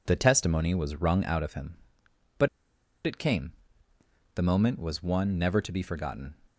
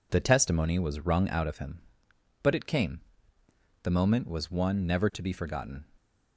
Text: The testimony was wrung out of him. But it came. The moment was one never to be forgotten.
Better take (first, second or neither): second